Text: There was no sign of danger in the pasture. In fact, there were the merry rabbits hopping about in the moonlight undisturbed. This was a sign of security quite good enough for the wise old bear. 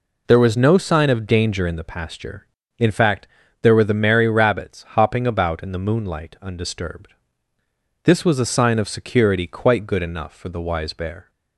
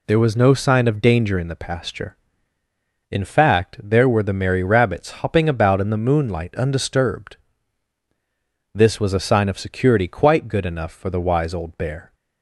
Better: second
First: skips "old"; at 10.9 s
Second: none

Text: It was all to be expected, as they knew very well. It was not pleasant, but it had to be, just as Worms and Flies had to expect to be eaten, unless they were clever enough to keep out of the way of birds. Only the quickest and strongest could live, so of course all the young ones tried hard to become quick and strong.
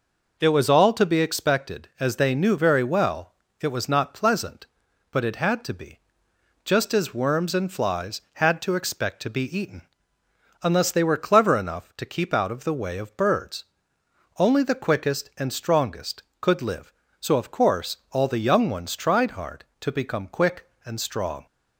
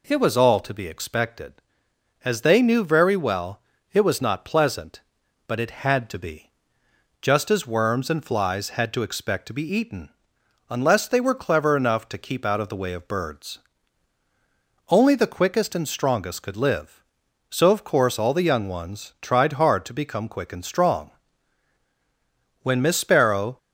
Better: first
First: none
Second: goes on to say "When Miss Sparrow"; noticeable; from 22.6 s on; 0.96 s long

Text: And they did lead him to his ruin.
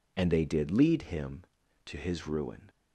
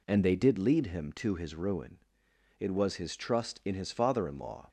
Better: first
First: none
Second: goes on to say "It was his trust in his father in law"; strong; from 2.5 s on; 2.0 s long

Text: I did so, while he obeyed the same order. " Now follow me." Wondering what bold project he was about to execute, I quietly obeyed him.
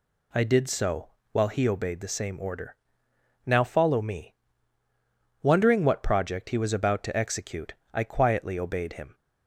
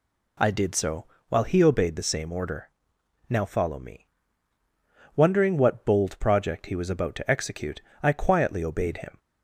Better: second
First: skips "bold"; at 6.0 s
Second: none

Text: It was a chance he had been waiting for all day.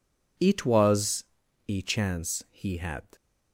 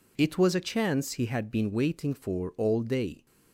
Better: second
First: pauses between "was" and "a"; at 1.2 s; 0.44 s long // stops before "been waiting for all day"; at 3.1 s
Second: none

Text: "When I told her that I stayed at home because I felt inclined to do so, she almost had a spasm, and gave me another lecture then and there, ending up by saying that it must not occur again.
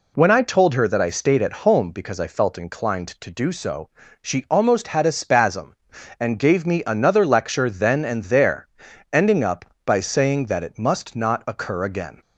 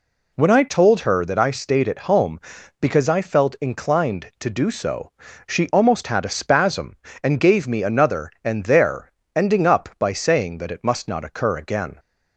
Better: first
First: none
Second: skips "lecture then"; at 8.3 s

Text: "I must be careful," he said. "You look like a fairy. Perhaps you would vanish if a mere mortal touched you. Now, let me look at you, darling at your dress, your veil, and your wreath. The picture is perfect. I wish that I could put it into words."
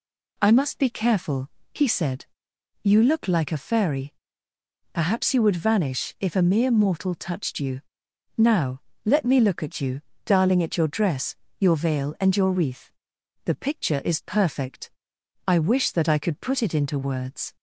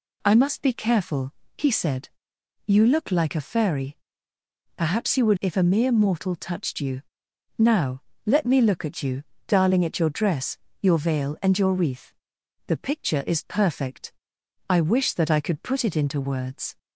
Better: first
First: none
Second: skips "vanish"; at 5.3 s

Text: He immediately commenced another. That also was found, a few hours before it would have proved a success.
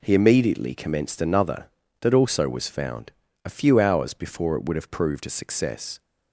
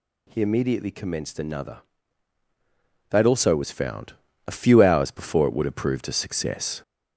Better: first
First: none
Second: gets louder; slight; throughout; 3.5 dB

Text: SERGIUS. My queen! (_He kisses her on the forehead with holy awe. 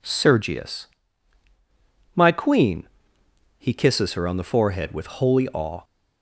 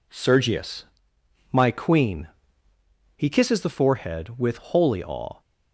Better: first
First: none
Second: skips "her on"; at 3.5 s

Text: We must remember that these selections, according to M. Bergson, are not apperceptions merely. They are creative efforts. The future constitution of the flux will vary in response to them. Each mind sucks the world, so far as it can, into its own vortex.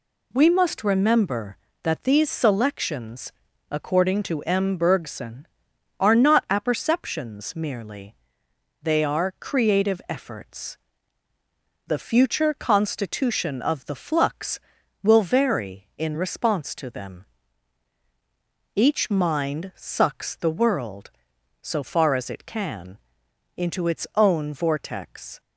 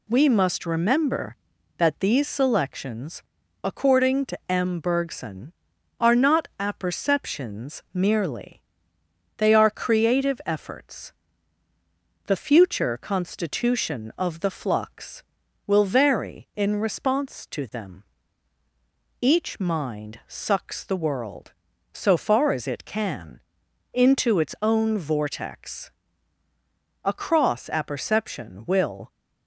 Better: first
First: none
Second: goes on to say "A cross apperception will"; strong; from 27.0 s on; 2.0 s long

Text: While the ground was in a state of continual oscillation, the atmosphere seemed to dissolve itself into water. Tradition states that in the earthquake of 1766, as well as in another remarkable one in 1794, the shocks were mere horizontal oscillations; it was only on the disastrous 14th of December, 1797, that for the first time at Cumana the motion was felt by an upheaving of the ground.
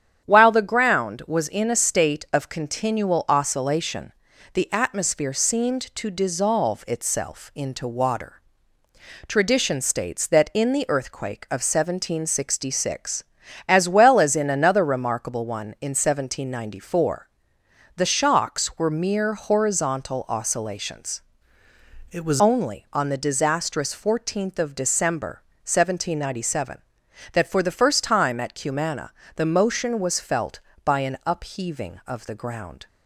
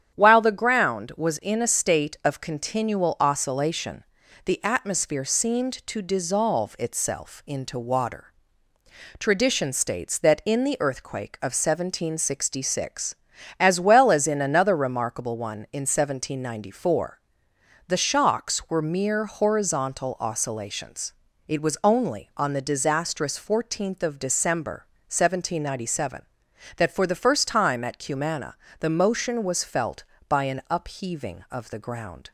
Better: second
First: starts louder than the rest; strong; until 1.3 s; 9 dB // changes voice from "it" to "was"; from 22.1 to 22.4 s; 0.3 s long // pauses between "Cumana" and "the"; slight; at 29.1 s; 0.24 s long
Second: starts louder than the rest; strong; until 1.2 s; 9 dB // pauses between "Cumana" and "the"; slight; at 28.5 s; 0.24 s long

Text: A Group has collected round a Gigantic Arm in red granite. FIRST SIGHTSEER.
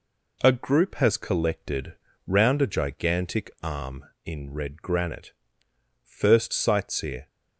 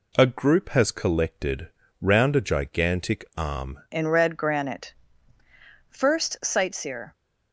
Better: first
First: pauses between "collected" and "round"; slight; at 1.9 s; 0.30 s long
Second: pauses between "collected" and "round"; slight; at 1.6 s; 0.30 s long // changes voice at "in"; from 3.9 s on; 3.2 s long

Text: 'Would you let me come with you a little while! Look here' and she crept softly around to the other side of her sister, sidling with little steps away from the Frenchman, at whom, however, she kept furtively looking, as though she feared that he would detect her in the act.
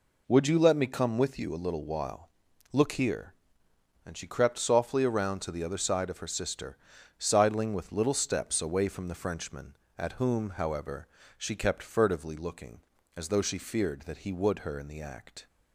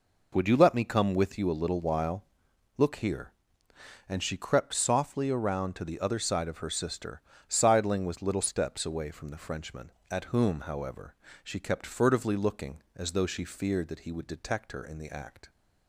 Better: second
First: skips "detect"; at 14.6 s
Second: none

